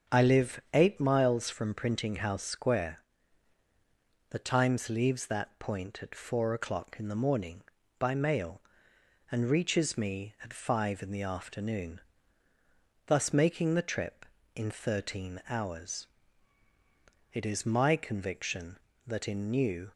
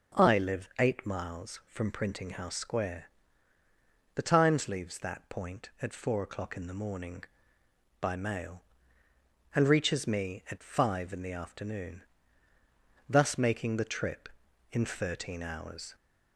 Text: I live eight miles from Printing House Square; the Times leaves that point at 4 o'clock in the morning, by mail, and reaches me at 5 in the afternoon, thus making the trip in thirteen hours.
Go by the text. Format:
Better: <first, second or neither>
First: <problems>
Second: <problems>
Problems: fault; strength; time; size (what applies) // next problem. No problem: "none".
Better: second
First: starts louder than the rest; until 1.2 s; 6.5 dB // goes on to say "It is my conviction that in New"; strong; from 17.3 s on; 2.5 s long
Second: none